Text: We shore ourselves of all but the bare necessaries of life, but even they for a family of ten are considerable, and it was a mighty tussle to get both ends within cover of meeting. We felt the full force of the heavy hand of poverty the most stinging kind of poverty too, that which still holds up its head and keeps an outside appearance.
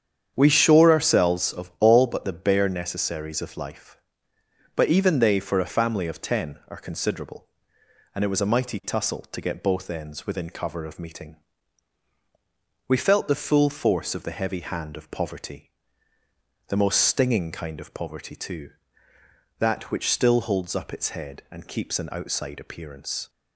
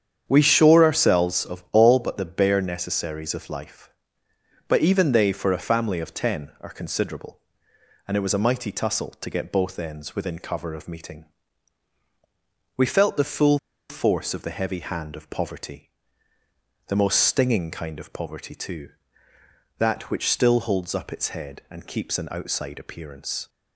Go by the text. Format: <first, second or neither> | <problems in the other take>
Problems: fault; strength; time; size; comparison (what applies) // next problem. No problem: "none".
first | starts louder than the rest; strong; until 1.2 s; 8 dB; strong in the first // pauses between "full" and "force"; slight; at 13.5 s; 0.31 s long // pauses between "poverty" and "the"; noticeable; at 15.9 s; 0.98 s long; noticeable in the first